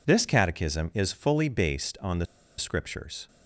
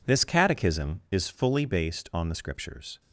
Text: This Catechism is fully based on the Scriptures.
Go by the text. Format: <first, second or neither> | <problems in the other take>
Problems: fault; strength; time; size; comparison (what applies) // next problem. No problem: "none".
second | pauses between "the" and "Scriptures"; slight; at 2.2 s; 0.33 s long